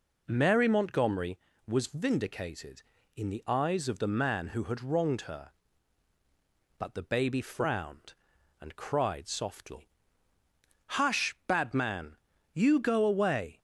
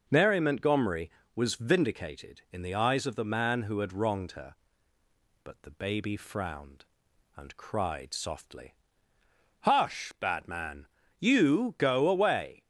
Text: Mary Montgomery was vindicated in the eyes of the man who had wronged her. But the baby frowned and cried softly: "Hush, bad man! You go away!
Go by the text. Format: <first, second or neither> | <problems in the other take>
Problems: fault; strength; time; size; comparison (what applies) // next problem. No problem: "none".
neither | none